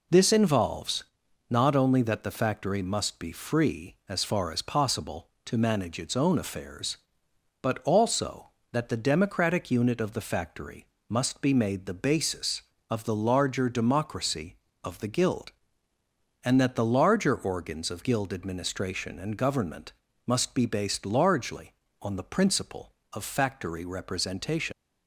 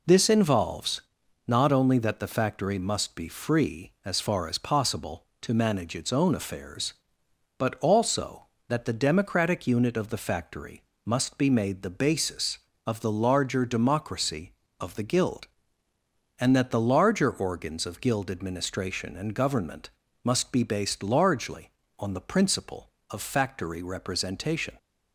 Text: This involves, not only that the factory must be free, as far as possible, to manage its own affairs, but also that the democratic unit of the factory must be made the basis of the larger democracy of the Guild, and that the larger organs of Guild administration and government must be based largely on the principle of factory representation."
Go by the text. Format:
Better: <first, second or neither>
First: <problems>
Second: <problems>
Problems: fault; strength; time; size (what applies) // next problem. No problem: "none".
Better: second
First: pauses between "factory" and "must"; slight; at 10.8 s; 0.24 s long // pauses between "government" and "must"; slight; at 19.9 s; 0.36 s long // leaves "representation" unfinished; at 24.7 s; 75 ms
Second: pauses between "factory" and "must"; slight; at 10.8 s; 0.24 s long // pauses between "government" and "must"; slight; at 19.8 s; 0.36 s long